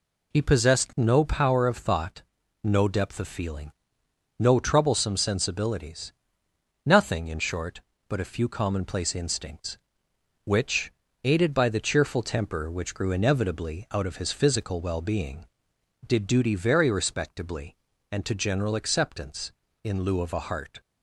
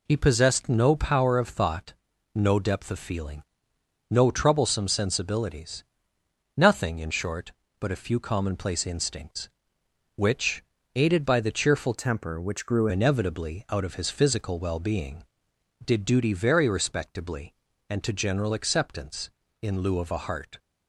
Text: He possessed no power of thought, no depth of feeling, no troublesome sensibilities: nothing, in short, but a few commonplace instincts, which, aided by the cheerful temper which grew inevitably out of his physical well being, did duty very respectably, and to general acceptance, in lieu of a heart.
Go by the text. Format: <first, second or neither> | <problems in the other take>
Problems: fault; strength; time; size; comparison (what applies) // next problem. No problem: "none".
first | changes voice from "temper" to "grew"; from 11.9 to 12.8 s; 0.9 s long